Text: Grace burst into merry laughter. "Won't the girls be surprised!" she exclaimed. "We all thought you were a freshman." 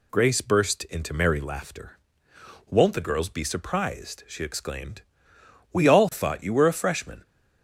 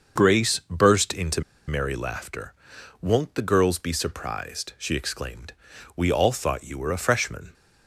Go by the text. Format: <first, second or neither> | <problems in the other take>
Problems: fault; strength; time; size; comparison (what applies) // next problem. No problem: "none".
first | starts louder than the rest; until 1.2 s; 6.5 dB // pauses between "into" and "merry"; slight; at 1.4 s; 0.25 s long